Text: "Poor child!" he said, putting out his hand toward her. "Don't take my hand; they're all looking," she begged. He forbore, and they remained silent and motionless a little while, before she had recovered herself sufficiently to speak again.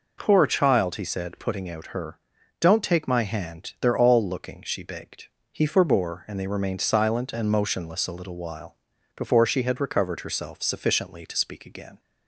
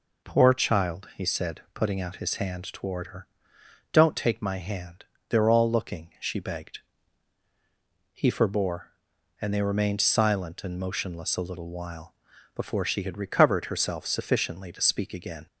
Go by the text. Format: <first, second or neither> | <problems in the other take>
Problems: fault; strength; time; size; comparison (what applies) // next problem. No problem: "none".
second | skips "his hand toward"; at 1.8 s